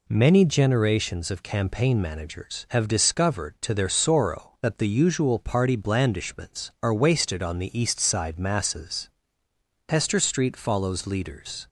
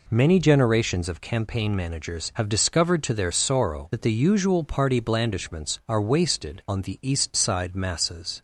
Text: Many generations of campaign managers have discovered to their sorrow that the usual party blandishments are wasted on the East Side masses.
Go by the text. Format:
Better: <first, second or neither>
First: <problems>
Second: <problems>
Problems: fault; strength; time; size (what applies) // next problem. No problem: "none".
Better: second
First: goes on to say "Hester Street follows leaders"; strong; from 9.8 s on; 1.7 s long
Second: none